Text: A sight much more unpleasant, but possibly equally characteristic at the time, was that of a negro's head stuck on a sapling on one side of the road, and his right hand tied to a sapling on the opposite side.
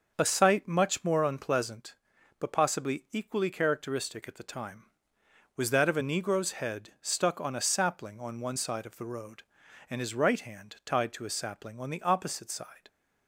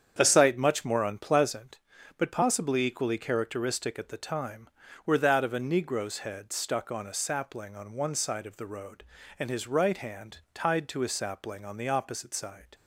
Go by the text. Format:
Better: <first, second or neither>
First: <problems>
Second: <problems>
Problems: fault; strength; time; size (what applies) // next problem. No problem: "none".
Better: first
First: none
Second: starts louder than the rest; strong; until 1.1 s; 8 dB // says "were" for "was"; at 5.0 s // pauses between "hand" and "tied"; slight; at 10.3 s; 0.15 s long